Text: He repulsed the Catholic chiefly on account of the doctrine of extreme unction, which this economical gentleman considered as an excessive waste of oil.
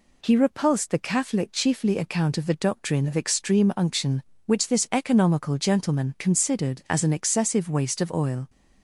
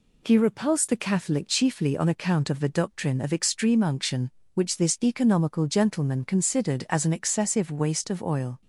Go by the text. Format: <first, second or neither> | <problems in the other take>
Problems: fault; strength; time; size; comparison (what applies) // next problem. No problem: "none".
second | skips "on"; at 1.9 s